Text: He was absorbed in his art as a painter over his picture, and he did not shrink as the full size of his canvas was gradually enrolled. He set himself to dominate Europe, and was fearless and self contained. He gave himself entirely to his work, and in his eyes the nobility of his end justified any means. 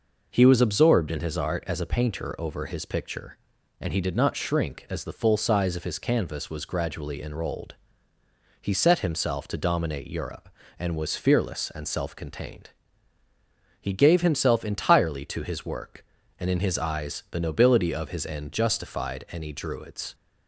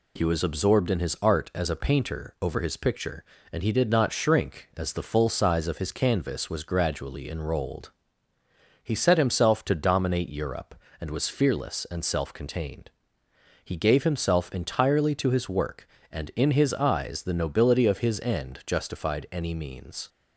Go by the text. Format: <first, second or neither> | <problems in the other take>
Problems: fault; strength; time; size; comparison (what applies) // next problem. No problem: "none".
second | says "druids" for "means"; at 19.5 s